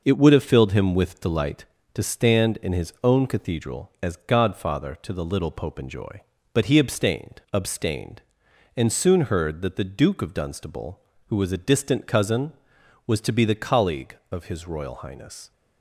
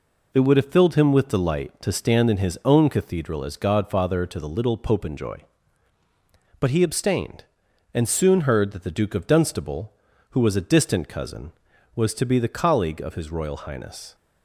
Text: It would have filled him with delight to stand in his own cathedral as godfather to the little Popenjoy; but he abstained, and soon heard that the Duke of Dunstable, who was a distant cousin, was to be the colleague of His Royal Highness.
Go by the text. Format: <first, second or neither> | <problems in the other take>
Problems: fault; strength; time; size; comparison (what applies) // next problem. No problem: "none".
second | says "abstained" twice; at 7.5 s